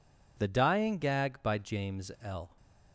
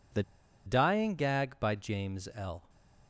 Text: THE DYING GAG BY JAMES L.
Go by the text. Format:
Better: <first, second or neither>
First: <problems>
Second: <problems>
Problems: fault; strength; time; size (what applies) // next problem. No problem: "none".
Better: first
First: none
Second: pauses between "THE" and "DYING"; at 0.2 s; 0.44 s long // stays silent after the last word; slight; from 2.5 s on; 0.5 s long